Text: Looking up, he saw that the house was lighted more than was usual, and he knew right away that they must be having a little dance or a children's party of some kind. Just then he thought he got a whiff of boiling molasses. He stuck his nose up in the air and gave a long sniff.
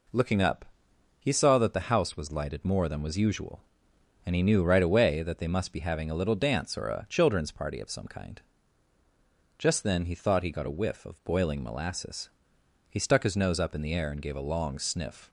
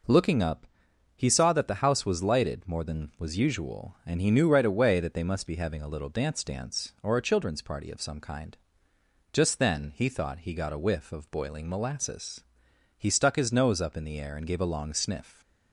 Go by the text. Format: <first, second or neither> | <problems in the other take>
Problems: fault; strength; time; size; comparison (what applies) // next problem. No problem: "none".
first | says "dance" twice; at 6.4 s